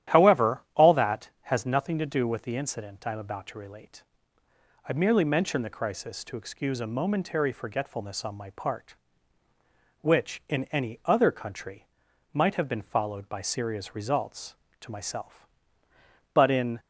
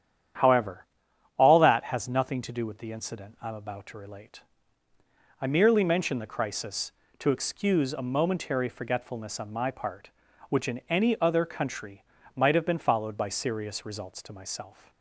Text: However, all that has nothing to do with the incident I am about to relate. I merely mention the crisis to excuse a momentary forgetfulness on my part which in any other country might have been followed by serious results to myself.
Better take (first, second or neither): second